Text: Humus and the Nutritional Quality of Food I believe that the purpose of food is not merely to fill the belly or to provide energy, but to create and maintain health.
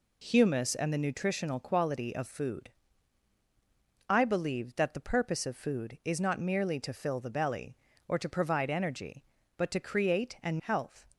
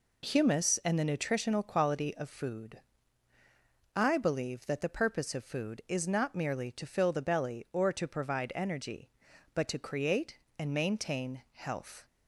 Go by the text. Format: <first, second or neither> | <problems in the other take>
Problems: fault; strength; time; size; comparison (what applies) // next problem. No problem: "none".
second | pauses between "Food" and "I"; strong; at 2.7 s; 1.3 s long; also in the second // skips "maintain"; at 10.5 s